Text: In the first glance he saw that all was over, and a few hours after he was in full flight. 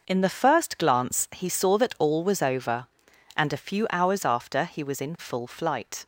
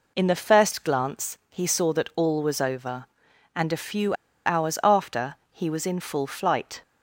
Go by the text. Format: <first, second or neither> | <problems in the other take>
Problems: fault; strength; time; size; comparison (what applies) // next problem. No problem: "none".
first | pauses between "few" and "hours"; slight; at 4.1 s; 0.32 s long // pauses between "after" and "he"; slight; at 5.3 s; 0.16 s long